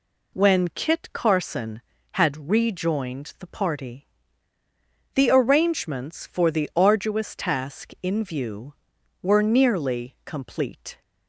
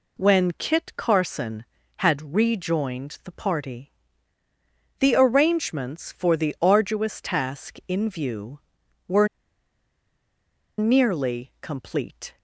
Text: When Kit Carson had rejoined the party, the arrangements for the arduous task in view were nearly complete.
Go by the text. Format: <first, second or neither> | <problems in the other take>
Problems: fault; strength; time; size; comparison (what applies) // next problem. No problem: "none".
first | pauses between "were" and "nearly"; strong; at 9.2 s; 1.5 s long